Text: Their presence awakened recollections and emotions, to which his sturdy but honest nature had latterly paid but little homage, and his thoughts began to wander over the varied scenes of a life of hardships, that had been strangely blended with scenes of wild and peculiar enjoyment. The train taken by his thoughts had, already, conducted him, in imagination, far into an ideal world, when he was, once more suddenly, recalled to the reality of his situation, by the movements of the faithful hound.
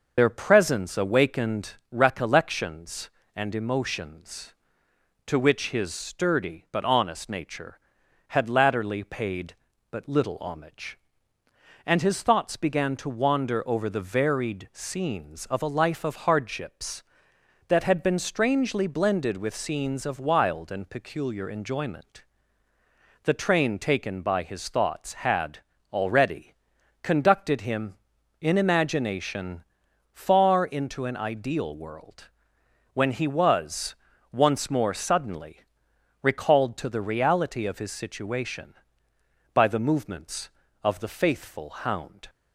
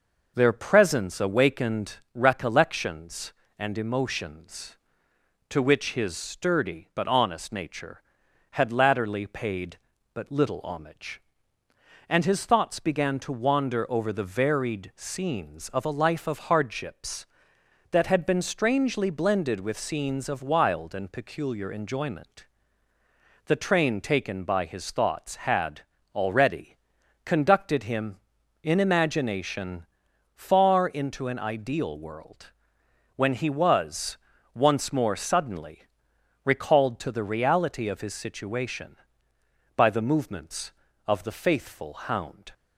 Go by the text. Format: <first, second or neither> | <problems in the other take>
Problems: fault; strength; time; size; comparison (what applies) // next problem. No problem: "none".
second | loses the start of "Their"; at 0.1 s; 50 ms